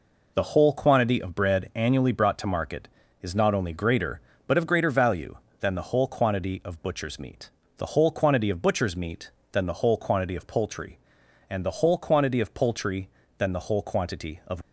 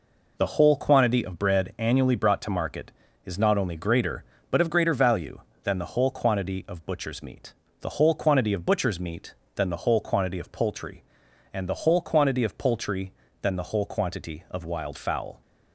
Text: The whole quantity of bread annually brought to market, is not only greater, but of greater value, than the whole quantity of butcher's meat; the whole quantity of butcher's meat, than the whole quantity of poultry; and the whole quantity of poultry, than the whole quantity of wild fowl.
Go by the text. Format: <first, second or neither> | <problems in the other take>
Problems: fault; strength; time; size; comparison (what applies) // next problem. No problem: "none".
second | stops before "wild fowl"; at 14.6 s